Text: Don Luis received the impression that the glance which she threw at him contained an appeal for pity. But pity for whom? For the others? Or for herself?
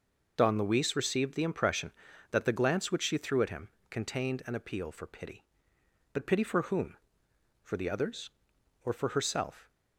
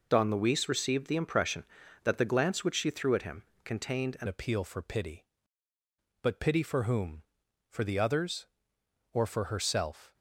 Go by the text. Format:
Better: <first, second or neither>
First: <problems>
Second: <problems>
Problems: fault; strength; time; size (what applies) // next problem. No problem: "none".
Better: first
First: pauses between "him" and "contained"; slight; at 3.6 s; 0.22 s long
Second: pauses between "him" and "contained"; slight; at 3.4 s; 0.22 s long // changes voice at "appeal"; from 4.2 s on; 5.9 s long